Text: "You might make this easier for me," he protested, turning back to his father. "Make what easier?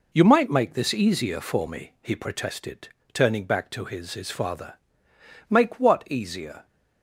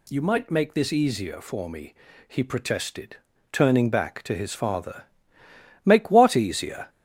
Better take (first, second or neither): second